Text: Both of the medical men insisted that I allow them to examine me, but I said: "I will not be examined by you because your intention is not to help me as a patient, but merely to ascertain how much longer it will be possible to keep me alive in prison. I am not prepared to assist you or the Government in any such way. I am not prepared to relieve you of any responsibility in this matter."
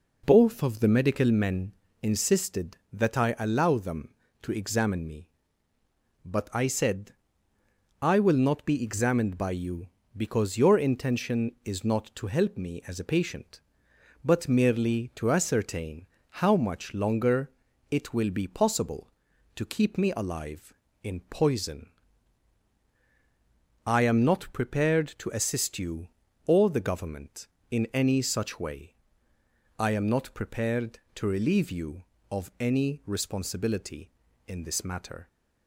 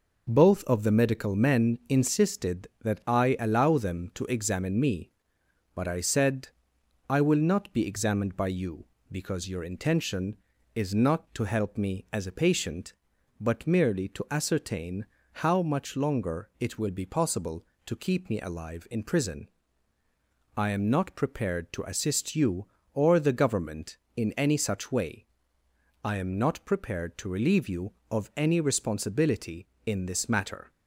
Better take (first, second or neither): second